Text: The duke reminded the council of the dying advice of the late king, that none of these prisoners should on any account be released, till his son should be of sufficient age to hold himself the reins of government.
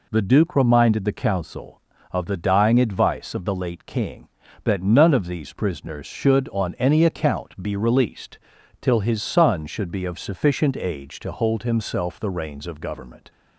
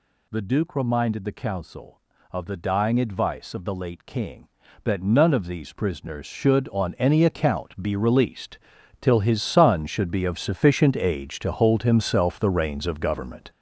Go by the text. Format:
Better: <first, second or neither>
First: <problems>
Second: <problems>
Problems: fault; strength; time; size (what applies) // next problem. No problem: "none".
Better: first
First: none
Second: gets louder; strong; throughout; 8.5 dB